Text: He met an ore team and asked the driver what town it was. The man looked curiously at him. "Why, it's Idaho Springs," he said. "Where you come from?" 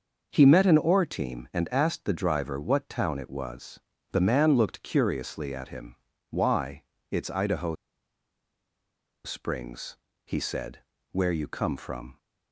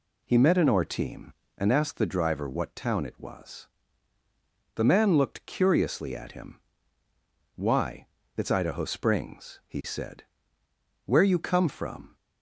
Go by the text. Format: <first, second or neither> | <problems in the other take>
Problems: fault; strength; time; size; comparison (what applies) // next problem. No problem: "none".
second | starts louder than the rest; noticeable; until 1.3 s; 6 dB // pauses between "Idaho" and "Springs"; strong; at 7.7 s; 1.5 s long